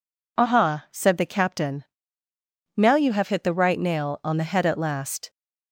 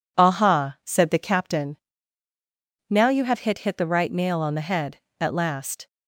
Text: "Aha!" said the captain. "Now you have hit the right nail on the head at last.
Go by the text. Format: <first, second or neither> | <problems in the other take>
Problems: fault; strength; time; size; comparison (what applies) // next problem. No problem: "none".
first | says "hit" twice; at 3.5 s